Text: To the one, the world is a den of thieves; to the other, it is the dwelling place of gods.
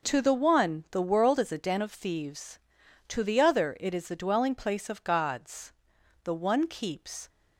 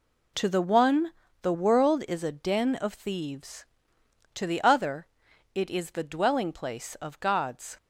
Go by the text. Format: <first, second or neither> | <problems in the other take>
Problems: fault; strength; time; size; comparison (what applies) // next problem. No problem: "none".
second | goes on to say "The one keeps"; noticeable; from 6.2 s on; 1.0 s long